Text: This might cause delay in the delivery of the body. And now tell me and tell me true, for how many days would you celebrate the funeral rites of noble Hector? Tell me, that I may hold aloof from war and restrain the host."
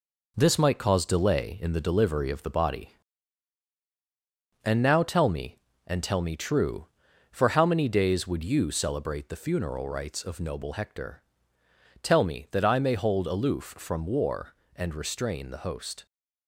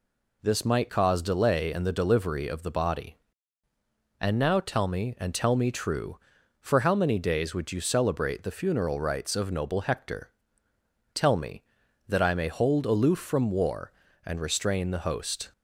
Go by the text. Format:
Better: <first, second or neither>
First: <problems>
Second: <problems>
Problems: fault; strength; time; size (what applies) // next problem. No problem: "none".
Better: second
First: gets quieter; noticeable; throughout; 6 dB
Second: none